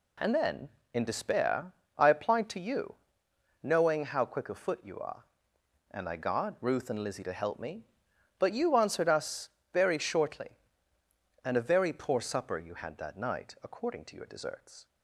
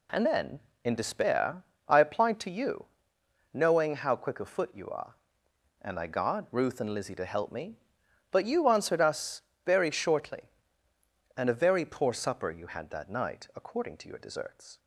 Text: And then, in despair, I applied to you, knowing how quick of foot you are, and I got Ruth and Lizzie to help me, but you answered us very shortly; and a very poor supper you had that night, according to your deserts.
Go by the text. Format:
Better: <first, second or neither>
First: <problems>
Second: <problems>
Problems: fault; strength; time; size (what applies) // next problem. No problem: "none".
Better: neither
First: pauses between "us" and "very"; slight; at 9.4 s; 0.24 s long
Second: pauses between "us" and "very"; slight; at 9.4 s; 0.24 s long